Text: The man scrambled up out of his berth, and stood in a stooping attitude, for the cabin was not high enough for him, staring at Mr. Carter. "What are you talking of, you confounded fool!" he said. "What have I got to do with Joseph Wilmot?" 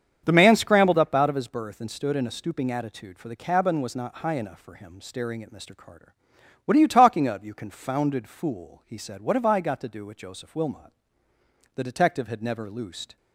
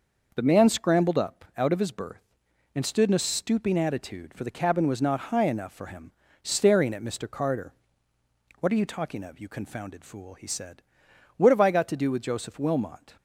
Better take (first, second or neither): second